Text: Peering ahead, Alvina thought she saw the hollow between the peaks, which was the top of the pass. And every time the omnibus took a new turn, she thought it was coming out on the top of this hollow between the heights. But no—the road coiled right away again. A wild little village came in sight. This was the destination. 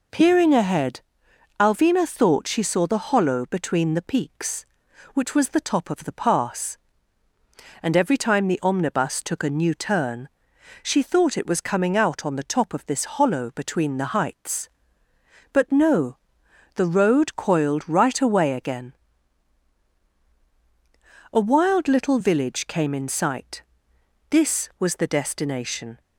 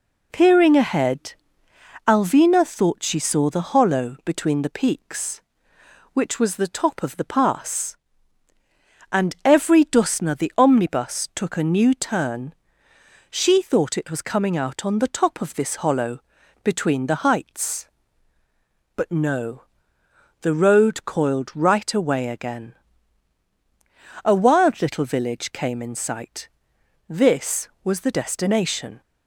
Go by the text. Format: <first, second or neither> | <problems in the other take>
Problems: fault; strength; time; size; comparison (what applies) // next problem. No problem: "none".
first | says "dusna" for "time"; at 9.8 s // pauses between "hollow" and "between"; at 16.2 s; 0.42 s long